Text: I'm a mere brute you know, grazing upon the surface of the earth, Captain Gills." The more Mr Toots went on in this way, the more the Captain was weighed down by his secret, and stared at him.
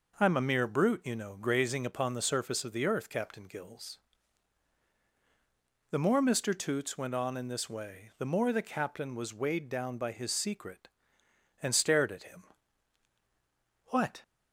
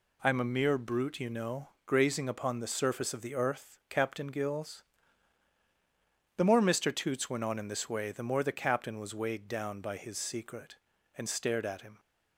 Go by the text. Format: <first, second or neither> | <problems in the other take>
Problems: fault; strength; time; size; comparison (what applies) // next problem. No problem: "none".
second | goes on to say "What"; slight; from 13.8 s on; 0.34 s long